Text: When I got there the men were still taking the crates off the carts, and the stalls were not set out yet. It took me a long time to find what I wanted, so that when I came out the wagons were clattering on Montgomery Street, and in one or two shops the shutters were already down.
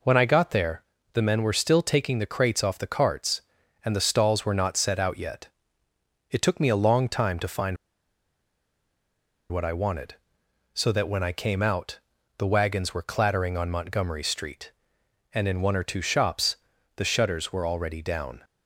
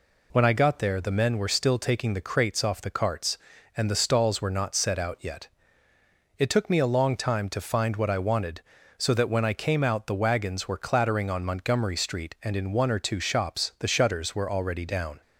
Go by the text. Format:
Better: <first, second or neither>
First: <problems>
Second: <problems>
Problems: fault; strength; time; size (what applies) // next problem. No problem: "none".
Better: second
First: pauses between "there" and "the"; slight; at 0.8 s; 0.30 s long // pauses between "find" and "what"; strong; at 7.7 s; 1.7 s long // pauses between "out" and "the"; at 11.9 s; 0.40 s long // pauses between "shops" and "the"; at 16.5 s; 0.38 s long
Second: none